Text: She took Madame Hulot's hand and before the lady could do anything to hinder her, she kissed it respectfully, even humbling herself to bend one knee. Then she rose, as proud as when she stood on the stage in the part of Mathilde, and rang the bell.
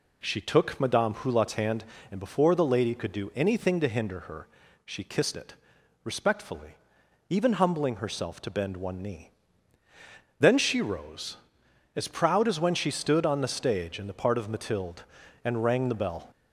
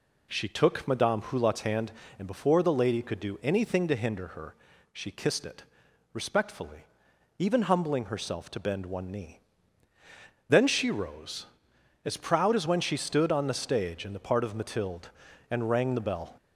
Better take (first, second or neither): neither